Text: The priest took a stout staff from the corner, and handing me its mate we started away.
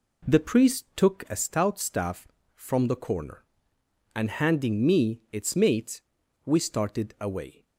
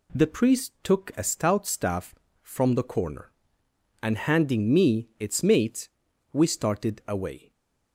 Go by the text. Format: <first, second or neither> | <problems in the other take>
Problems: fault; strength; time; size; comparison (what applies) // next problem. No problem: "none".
second | starts louder than the rest; slight; until 1.2 s; 2.5 dB // pauses between "mate" and "we"; noticeable; at 5.9 s; 0.46 s long; noticeable in the second